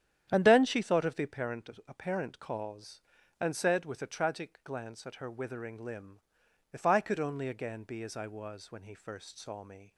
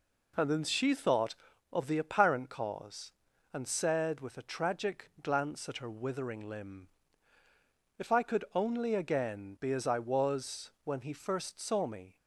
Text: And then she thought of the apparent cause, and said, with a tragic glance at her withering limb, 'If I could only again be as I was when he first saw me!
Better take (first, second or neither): second